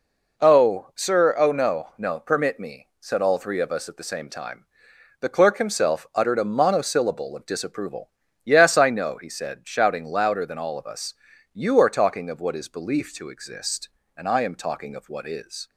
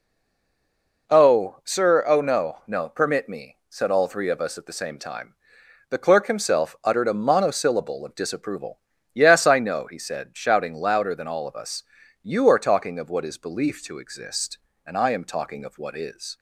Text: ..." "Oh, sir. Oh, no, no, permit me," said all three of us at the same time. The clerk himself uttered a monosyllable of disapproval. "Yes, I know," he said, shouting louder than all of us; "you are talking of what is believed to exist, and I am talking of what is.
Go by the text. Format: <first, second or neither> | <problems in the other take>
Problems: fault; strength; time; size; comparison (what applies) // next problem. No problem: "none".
first | stays silent before the first word; until 1.0 s; 1.0 s long